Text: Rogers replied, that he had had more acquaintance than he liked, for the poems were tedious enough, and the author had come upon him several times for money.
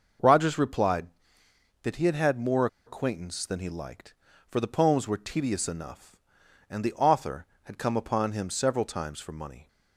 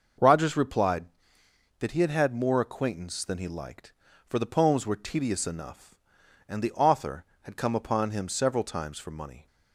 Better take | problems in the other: second | pauses between "more" and "acquaintance"; slight; at 2.6 s; 0.19 s long

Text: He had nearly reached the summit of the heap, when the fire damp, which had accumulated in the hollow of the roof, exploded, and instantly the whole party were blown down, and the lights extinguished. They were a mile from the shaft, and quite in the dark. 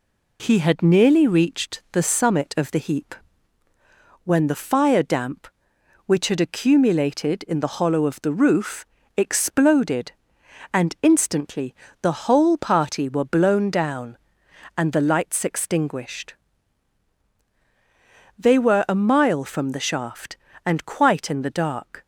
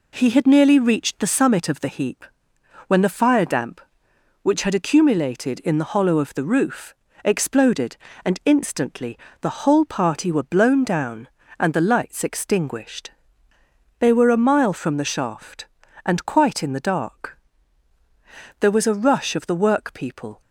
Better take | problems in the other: first | pauses between "instantly" and "the"; slight; at 9.1 s; 0.22 s long; slight in the first // goes on to say "There was a rush of the workpeople"; strong; from 18.5 s on; 1.8 s long

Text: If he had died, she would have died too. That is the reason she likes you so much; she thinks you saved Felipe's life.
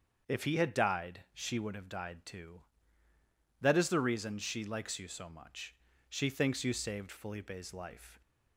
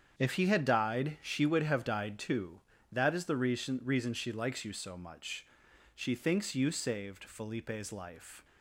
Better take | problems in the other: first | starts louder than the rest; strong; until 1.1 s; 7.5 dB; also in the first // says "reason" twice; at 3.8 s

